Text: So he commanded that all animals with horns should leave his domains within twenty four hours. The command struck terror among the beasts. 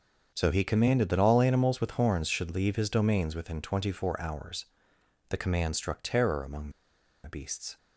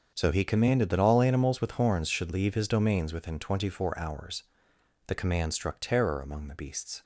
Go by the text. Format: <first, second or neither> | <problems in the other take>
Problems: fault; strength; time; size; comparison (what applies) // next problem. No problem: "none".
second | starts louder than the rest; until 1.3 s; 7 dB; also in the second // pauses between "among" and "the"; noticeable; at 6.7 s; 0.53 s long